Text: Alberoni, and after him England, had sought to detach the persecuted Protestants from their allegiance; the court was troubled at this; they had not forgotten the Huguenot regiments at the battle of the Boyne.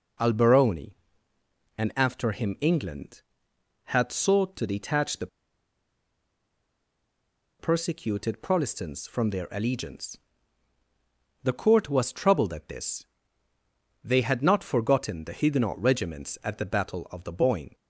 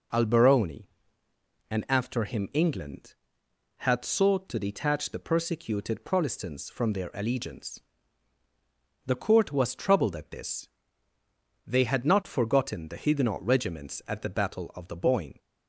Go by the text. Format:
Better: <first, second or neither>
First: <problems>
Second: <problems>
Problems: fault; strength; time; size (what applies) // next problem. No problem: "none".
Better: second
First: pauses between "the" and "persecuted"; strong; at 5.2 s; 2.3 s long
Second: none